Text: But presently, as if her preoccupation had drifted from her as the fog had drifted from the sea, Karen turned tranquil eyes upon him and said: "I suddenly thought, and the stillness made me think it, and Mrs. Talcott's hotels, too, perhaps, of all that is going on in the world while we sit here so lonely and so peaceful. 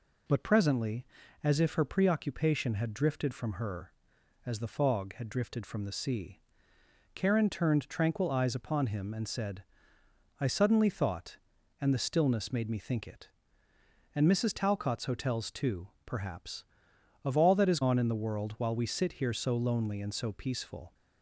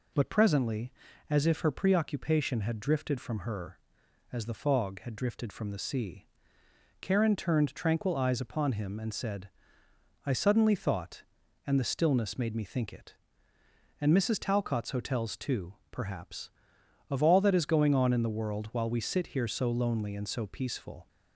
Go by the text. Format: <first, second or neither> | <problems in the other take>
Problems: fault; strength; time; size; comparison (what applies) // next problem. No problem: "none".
second | skips "going"; at 17.8 s